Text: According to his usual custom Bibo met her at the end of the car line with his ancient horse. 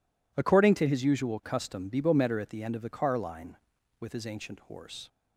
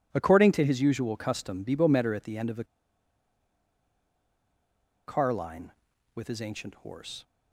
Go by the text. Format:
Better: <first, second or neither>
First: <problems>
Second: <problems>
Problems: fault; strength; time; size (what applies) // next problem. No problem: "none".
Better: first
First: none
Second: pauses between "the" and "car"; strong; at 2.6 s; 2.4 s long